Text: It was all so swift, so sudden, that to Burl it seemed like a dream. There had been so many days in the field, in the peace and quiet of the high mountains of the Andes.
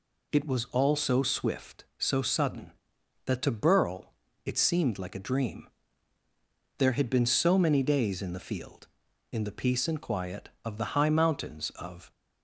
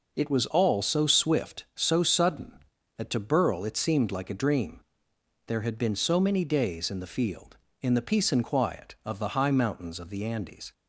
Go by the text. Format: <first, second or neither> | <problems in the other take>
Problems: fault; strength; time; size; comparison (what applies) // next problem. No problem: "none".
second | pauses between "Burl" and "it"; slight; at 4.1 s; 0.34 s long // stops before "the Andes"; at 12.1 s